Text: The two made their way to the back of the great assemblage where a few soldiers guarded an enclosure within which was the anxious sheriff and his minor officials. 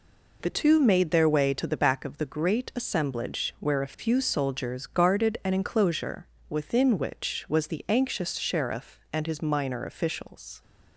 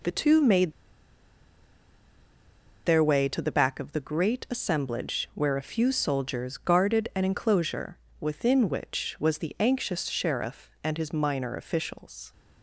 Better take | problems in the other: first | pauses between "made" and "their"; strong; at 0.7 s; 2.1 s long // pauses between "enclosure" and "within"; slight; at 7.9 s; 0.24 s long; slight in the first

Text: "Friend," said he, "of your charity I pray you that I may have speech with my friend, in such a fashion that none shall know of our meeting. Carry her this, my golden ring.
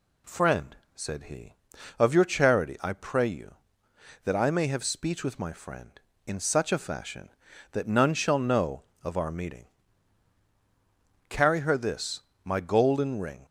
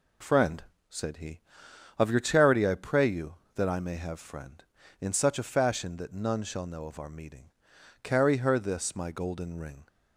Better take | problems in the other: first | skips "speech with my"; at 4.1 s

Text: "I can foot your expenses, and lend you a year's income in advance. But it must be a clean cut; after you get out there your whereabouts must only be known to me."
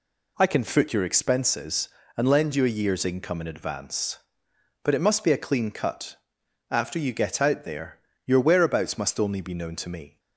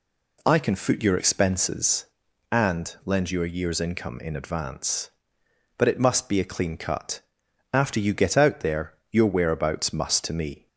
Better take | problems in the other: first | pauses between "there" and "your"; slight; at 8.9 s; 0.18 s long; slight in the first // skips "only be known"; at 10.2 s

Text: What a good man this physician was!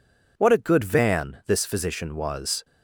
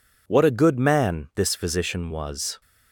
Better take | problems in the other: second | says "van" for "man"; at 0.8 s

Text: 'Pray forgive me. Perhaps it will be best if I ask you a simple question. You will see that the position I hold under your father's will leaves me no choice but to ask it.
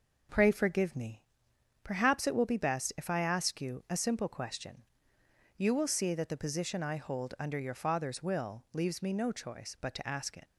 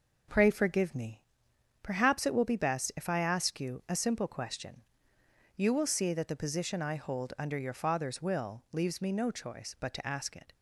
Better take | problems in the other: second | leaves "it" unfinished; at 10.4 s; 80 ms

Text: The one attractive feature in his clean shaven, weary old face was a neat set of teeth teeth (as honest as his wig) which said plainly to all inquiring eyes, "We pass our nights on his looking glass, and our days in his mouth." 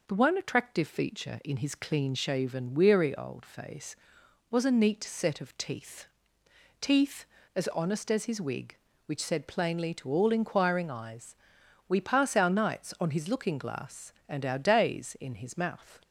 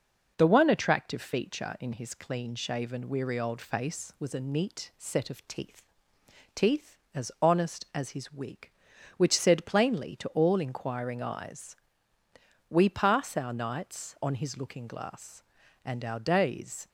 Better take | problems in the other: first | pauses between "teeth" and "teeth"; noticeable; at 5.8 s; 0.74 s long; noticeable in the first // stops before "in his mouth"; at 16.8 s

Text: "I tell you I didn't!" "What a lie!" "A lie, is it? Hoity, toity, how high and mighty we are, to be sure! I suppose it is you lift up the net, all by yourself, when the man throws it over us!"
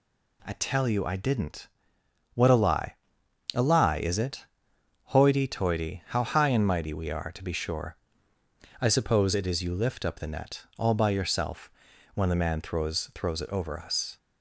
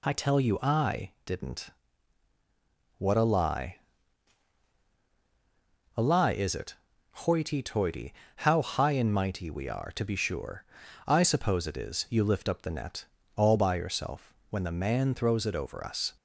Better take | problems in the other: second | says "throws" twice; at 13.1 s

